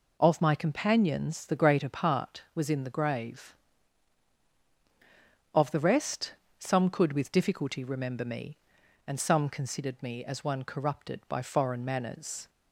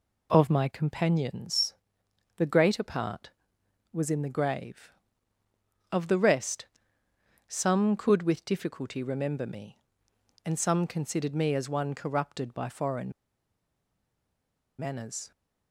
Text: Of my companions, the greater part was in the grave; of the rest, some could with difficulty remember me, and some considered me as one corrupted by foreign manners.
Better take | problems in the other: first | pauses between "foreign" and "manners"; strong; at 13.1 s; 1.6 s long

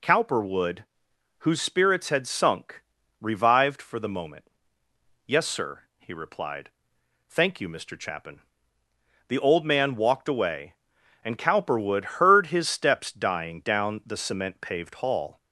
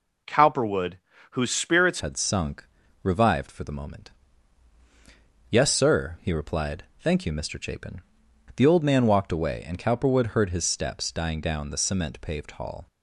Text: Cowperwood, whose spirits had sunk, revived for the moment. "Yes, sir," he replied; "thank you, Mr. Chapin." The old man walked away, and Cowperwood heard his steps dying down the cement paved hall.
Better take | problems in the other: first | changes voice at "had"; from 1.9 s on; 10.9 s long

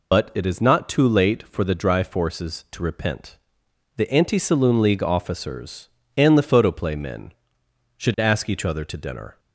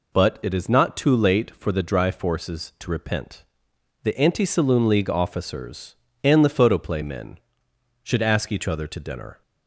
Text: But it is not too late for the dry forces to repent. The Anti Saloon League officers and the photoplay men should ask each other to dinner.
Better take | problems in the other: second | loses the start of "But"; at 0.1 s; 60 ms

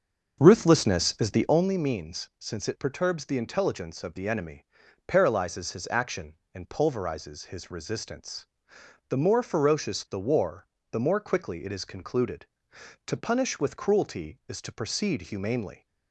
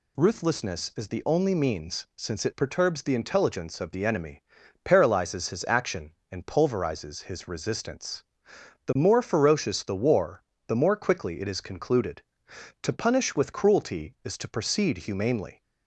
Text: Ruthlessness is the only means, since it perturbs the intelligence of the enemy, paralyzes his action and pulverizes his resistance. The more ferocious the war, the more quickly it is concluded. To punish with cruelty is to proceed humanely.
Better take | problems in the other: second | starts louder than the rest; until 1.7 s; 6.5 dB

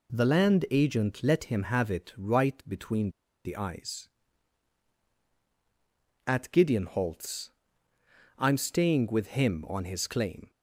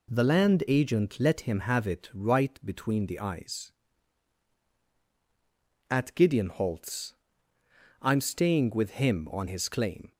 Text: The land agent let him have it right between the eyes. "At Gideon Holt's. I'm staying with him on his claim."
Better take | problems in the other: second | pauses between "between" and "the"; slight; at 3.1 s; 0.34 s long

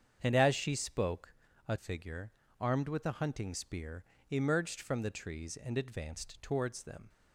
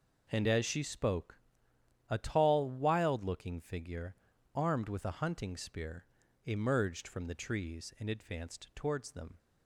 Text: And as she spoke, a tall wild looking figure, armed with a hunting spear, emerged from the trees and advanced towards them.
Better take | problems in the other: second | starts louder than the rest; strong; until 1.2 s; 7.5 dB // skips "tall wild looking"; at 1.7 s

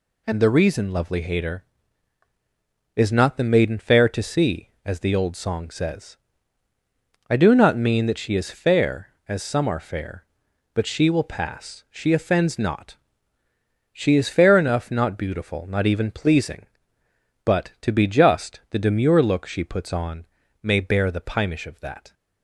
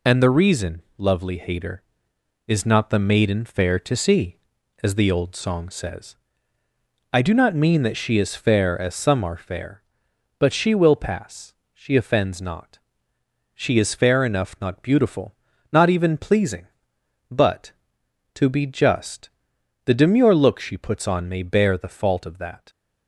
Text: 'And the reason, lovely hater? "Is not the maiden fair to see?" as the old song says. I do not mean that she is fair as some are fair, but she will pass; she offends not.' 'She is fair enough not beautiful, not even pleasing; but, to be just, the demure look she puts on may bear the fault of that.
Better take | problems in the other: second | pauses between "on" and "may"; slight; at 20.2 s; 0.36 s long // says "pimish" for "fault"; at 21.2 s

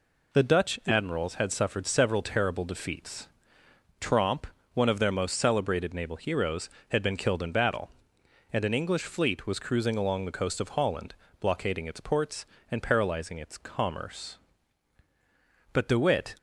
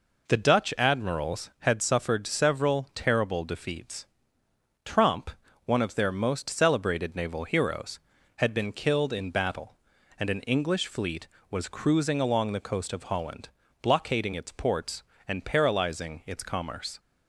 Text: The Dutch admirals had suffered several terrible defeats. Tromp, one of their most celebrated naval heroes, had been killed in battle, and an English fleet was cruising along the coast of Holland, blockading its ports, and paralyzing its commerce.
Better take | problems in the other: second | goes on to say "But De Witt"; noticeable; from 15.7 s on; 0.61 s long

